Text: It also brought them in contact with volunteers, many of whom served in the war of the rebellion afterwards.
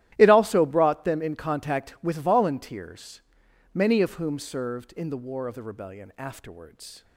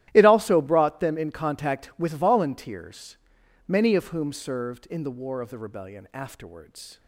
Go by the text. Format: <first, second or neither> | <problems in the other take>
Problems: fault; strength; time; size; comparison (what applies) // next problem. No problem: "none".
neither | starts louder than the rest; strong; the same in both